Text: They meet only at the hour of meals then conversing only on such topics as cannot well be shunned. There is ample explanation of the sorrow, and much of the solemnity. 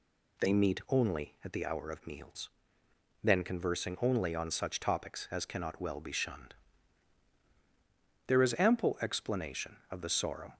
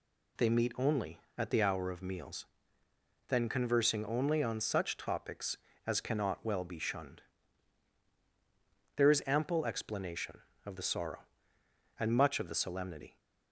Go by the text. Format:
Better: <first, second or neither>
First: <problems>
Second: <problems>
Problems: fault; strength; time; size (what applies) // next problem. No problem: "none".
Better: second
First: pauses between "meals" and "then"; noticeable; at 2.4 s; 0.74 s long // stops before "and much of the solemnity"; at 10.5 s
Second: pauses between "meals" and "then"; noticeable; at 2.4 s; 0.82 s long